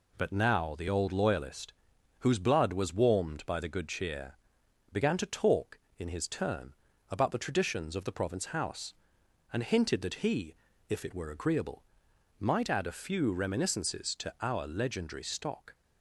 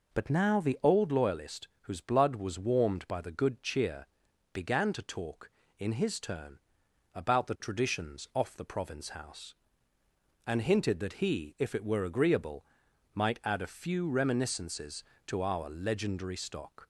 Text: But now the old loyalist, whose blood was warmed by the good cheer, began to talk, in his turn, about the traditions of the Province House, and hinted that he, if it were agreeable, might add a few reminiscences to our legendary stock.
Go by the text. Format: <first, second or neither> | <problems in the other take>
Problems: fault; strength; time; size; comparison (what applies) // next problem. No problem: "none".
first | says "off" for "of"; at 8.3 s